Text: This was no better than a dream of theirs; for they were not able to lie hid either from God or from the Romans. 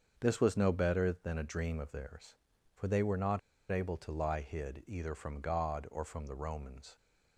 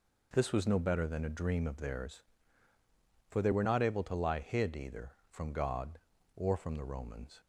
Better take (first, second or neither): second